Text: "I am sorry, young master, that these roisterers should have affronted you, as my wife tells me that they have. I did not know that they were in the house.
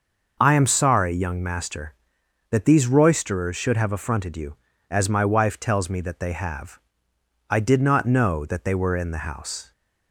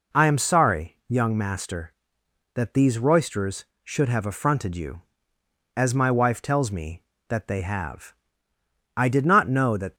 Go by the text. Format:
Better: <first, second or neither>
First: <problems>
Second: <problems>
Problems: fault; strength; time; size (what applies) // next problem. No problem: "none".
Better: first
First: none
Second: stops before "they were in the house"; at 9.9 s